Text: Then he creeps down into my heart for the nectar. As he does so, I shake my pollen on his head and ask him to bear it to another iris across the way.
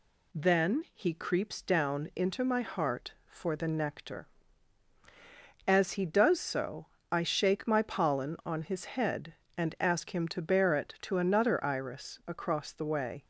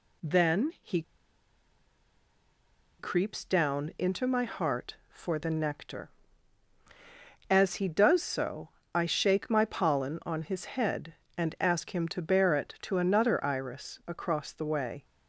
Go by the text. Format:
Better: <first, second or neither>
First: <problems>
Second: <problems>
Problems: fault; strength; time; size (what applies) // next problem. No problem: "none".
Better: first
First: none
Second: pauses between "he" and "creeps"; strong; at 1.0 s; 1.9 s long